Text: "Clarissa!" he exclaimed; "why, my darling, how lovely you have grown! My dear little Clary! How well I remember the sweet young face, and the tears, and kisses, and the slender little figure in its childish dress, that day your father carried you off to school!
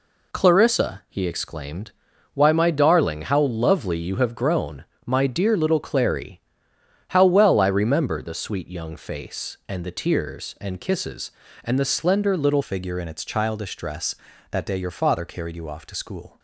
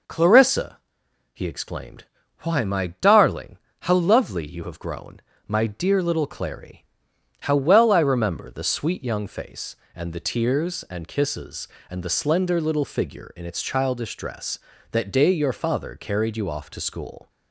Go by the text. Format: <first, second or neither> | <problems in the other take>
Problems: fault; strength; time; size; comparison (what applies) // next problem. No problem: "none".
second | changes voice at "figure"; from 12.6 s on; 3.7 s long